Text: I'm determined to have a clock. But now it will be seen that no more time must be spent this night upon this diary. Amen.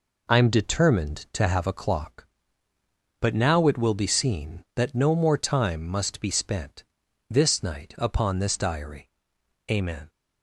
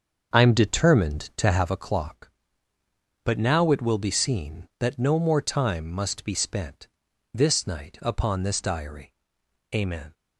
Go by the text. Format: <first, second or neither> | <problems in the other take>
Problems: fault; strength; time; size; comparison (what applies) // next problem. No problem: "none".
first | starts louder than the rest; until 1.7 s; 6.5 dB // pauses between "spent" and "this"; noticeable; at 6.8 s; 0.46 s long; noticeable in the first